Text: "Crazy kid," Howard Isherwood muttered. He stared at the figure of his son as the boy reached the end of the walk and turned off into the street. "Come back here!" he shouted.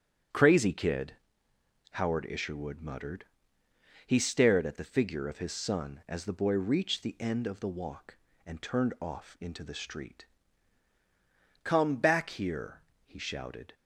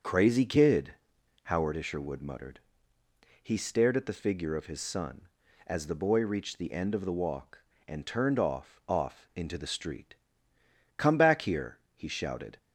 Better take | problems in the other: first | starts louder than the rest; until 1.5 s; 7 dB; strong in the first // says "off" twice; at 8.8 s

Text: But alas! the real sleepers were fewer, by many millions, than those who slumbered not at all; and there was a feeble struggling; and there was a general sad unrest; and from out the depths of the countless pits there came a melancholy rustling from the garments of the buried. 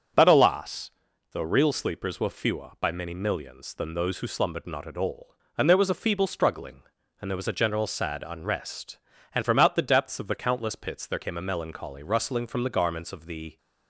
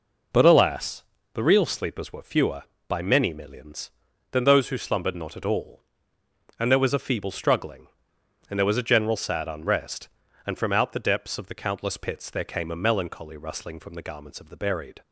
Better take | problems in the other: second | starts louder than the rest; noticeable; until 1.5 s; 6 dB // stops before "buried"; at 13.5 s

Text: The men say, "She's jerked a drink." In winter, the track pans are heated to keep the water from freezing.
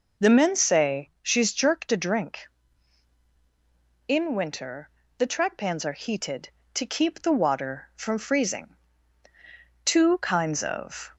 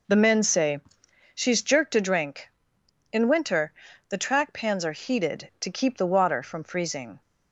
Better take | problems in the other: second | goes on to say "Two kinds of"; noticeable; from 9.8 s on; 1.3 s long

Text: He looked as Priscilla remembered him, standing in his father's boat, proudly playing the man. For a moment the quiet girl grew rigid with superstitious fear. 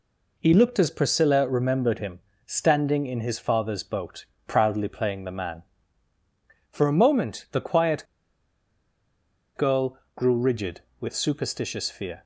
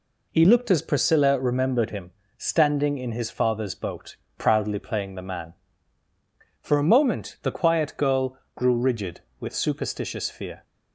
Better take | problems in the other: second | pauses between "quiet" and "girl"; strong; at 8.0 s; 1.5 s long // pauses between "girl" and "grew"; slight; at 9.9 s; 0.18 s long; slight in the second

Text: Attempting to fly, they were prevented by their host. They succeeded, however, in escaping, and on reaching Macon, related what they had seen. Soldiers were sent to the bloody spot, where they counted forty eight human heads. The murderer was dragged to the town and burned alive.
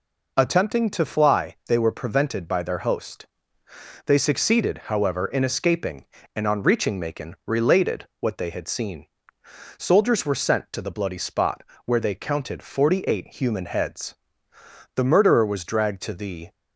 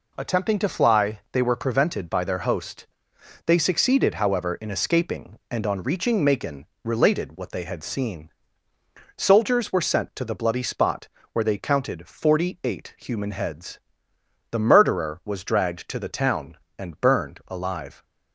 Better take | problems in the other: second | stops before "town and burned alive"; at 16.5 s

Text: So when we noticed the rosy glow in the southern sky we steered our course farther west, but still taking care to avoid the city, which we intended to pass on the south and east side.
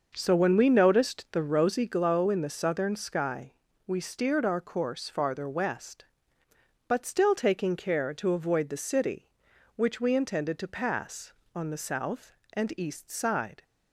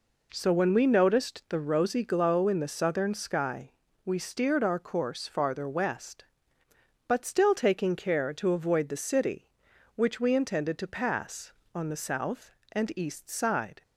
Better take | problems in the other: second | starts louder than the rest; until 2.0 s; 6 dB // pauses between "sky" and "we"; slight; at 3.5 s; 0.34 s long; slight in the second

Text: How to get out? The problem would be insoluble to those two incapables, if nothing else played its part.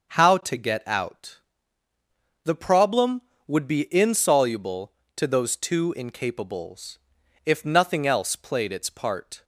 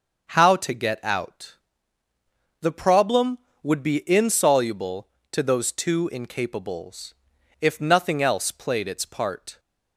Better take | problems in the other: neither | starts louder than the rest; the same in both

